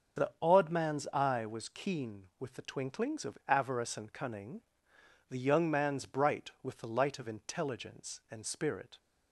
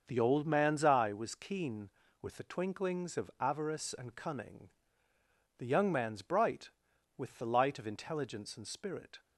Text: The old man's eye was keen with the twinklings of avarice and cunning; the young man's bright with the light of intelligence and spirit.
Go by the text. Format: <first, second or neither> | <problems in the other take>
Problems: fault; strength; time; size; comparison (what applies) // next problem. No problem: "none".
second | starts louder than the rest; until 1.3 s; 7 dB; also in the second // says "odd" for "old"; at 0.4 s